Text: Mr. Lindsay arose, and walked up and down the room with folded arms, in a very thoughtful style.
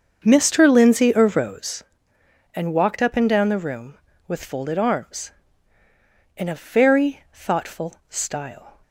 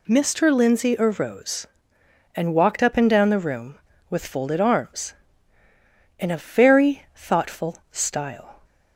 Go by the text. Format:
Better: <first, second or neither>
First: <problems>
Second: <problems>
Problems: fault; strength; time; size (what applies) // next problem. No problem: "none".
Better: second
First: starts louder than the rest; until 1.7 s; 7 dB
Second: none